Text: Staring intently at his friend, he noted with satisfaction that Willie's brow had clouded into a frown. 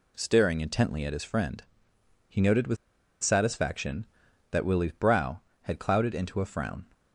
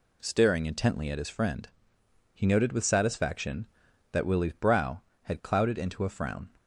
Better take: second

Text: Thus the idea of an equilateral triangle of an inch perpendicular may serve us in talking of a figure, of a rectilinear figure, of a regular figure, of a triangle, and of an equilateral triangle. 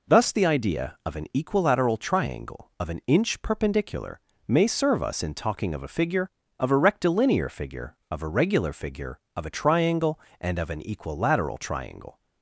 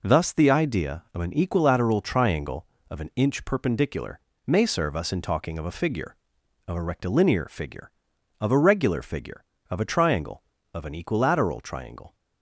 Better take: first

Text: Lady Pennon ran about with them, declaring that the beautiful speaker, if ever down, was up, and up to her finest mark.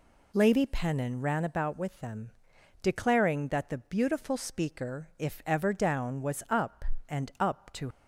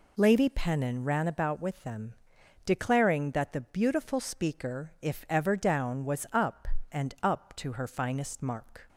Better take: second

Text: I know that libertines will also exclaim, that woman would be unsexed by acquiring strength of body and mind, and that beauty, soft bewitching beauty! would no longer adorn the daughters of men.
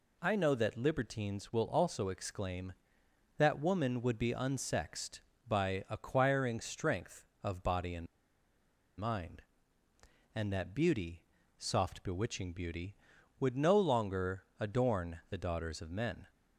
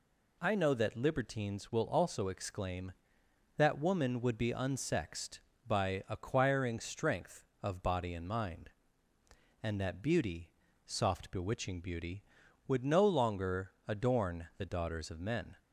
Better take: second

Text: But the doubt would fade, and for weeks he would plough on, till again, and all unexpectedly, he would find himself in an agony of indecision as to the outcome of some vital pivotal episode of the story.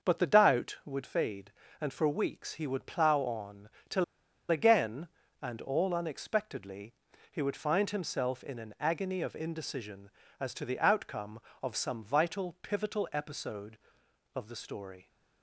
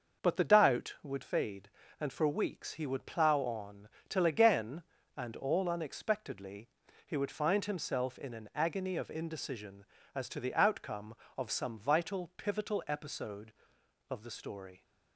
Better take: second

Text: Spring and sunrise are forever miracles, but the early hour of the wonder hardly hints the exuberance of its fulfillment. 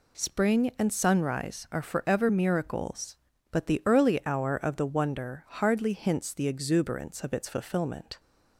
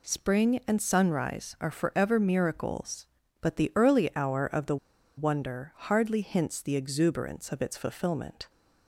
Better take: first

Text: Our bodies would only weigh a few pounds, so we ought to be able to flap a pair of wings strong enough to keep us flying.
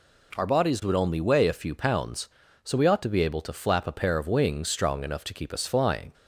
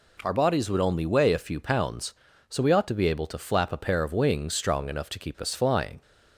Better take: neither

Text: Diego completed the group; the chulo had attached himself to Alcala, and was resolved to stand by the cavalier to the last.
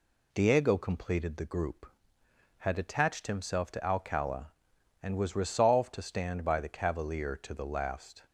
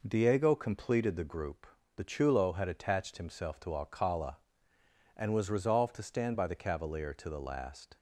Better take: second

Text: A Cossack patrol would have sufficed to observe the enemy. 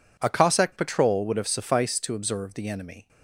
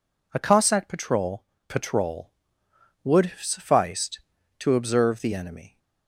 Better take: first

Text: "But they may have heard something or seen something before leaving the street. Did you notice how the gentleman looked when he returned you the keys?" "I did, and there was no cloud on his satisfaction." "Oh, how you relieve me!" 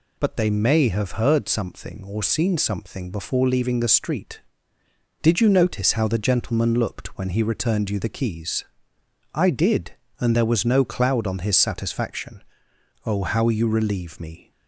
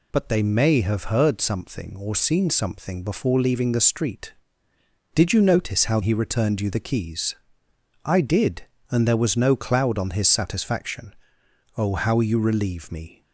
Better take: first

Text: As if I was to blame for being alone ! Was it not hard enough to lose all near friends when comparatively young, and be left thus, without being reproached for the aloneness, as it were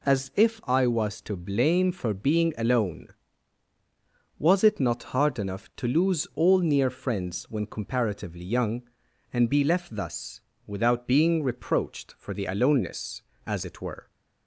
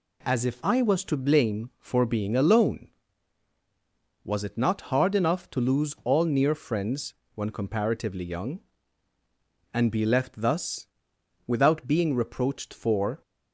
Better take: first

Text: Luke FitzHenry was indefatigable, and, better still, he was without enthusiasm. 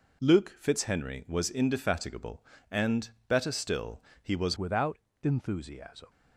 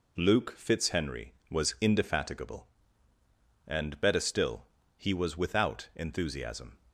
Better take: second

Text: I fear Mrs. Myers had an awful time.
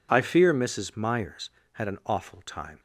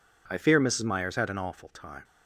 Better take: neither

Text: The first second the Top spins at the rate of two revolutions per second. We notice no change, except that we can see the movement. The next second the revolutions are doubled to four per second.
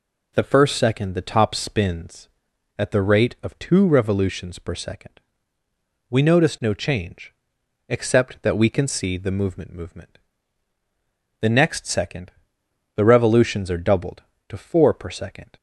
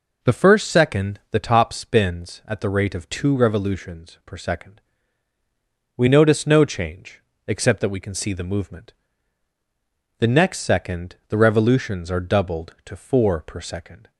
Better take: second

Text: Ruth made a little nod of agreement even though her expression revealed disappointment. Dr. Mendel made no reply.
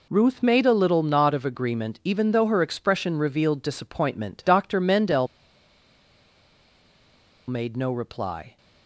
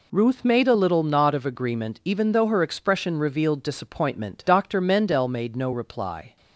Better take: second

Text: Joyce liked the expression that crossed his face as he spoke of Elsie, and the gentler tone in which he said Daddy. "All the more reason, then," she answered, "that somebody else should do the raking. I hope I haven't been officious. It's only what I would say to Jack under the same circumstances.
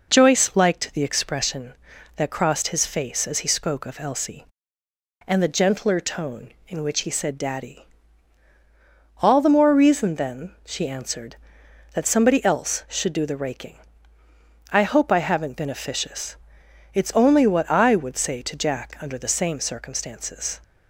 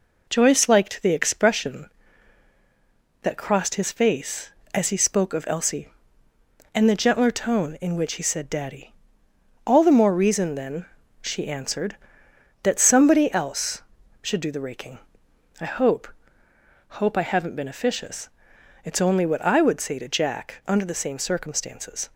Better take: first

